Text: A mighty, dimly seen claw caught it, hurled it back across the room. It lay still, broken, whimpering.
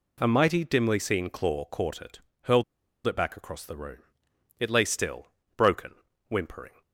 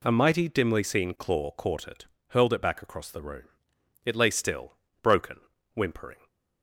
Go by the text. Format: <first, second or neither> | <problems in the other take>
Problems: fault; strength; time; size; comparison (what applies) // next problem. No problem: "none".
second | pauses between "hurled" and "it"; at 2.6 s; 0.43 s long